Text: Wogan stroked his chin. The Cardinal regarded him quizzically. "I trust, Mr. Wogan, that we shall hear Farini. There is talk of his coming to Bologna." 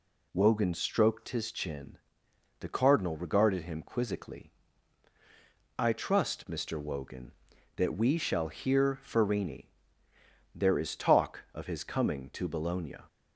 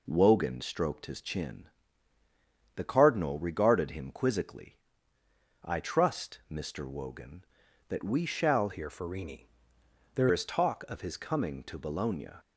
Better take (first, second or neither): first